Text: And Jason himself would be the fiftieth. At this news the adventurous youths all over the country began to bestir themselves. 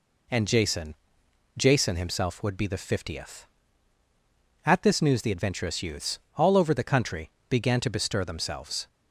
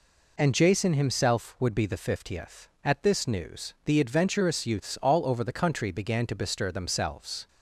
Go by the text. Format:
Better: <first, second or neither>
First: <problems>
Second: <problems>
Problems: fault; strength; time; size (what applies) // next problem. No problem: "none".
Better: second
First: says "Jason" twice; at 1.5 s // pauses between "youths" and "all"; slight; at 6.1 s; 0.18 s long // pauses between "country" and "began"; slight; at 7.2 s; 0.18 s long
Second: none